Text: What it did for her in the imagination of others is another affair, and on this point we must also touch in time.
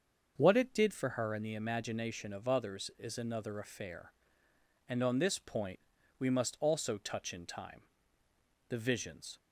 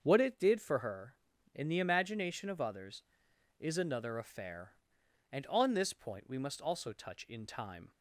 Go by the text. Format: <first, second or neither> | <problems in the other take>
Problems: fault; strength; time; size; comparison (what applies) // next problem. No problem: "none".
second | starts louder than the rest; until 1.3 s; 6.5 dB; also in the second // pauses between "point" and "we"; at 5.7 s; 0.40 s long // goes on to say "The visions"; noticeable; from 8.6 s on; 0.70 s long